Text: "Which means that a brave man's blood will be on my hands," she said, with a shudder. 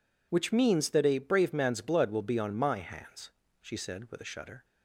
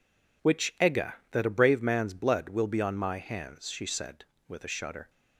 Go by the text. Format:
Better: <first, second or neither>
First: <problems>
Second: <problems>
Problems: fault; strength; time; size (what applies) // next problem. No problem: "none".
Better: first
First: none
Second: says "egga" for "means"; at 0.7 s